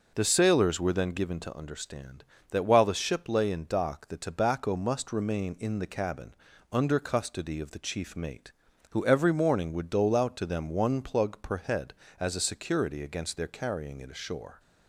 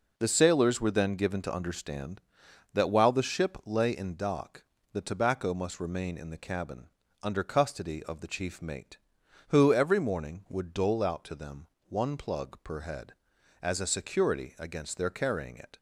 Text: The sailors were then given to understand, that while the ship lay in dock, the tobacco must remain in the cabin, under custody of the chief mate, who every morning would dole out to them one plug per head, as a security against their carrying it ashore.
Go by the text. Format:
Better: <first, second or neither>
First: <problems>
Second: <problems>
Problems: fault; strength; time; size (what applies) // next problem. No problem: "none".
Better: first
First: none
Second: pauses between "them" and "one"; slight; at 11.6 s; 0.22 s long // stops before "ashore"; at 15.7 s